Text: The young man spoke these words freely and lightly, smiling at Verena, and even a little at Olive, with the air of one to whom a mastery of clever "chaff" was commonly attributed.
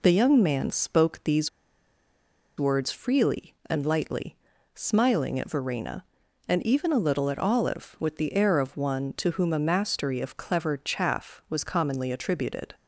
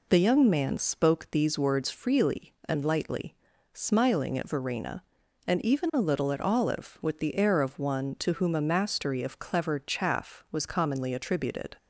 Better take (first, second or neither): second